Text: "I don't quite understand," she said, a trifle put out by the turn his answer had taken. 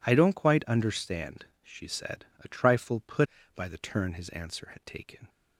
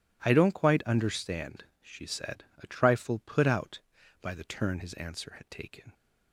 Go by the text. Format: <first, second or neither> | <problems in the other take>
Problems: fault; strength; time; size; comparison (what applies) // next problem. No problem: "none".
second | skips "out"; at 3.4 s